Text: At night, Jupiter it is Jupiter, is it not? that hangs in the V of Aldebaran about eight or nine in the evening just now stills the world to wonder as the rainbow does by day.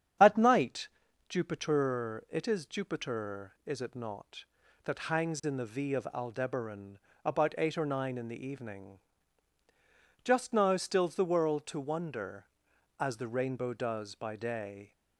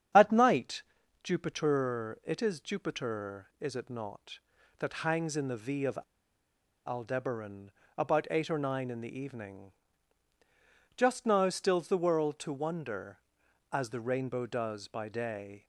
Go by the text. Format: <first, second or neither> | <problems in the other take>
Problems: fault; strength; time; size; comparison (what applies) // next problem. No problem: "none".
first | starts louder than the rest; strong; until 1.5 s; 8.5 dB; strong in the first // pauses between "of" and "Aldebaran"; noticeable; at 5.9 s; 0.89 s long // pauses between "Aldebaran" and "about"; slight; at 7.7 s; 0.26 s long; slight in the first // pauses between "evening" and "just"; at 9.7 s; 1.2 s long; also in the first